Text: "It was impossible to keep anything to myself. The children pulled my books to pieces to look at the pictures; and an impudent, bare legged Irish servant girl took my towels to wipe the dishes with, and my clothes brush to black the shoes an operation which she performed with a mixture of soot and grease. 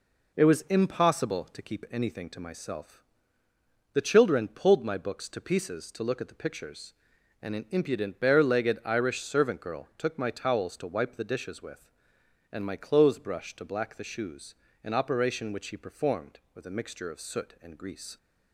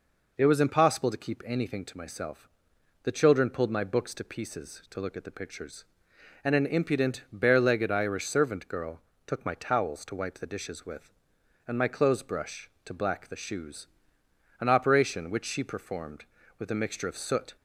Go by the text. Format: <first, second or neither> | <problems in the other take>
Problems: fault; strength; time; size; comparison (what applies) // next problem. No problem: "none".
first | pauses between "girl" and "took"; slight; at 9.0 s; 0.24 s long // pauses between "shoes" and "an"; noticeable; at 13.8 s; 0.70 s long; slight in the first // stops before "and grease"; at 17.5 s